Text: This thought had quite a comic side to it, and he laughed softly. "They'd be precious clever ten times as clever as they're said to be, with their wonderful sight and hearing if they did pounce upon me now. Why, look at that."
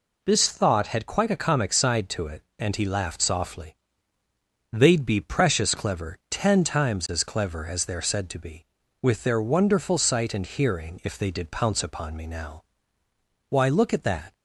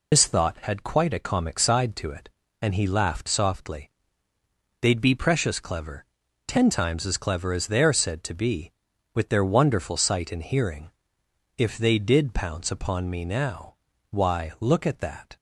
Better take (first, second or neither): first